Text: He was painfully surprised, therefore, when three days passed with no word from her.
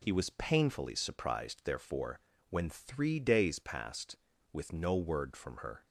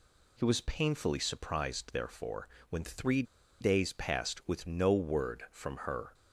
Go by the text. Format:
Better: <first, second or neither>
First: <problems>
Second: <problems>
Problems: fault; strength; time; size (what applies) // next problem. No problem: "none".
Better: first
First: none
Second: pauses between "three" and "days"; at 3.2 s; 0.38 s long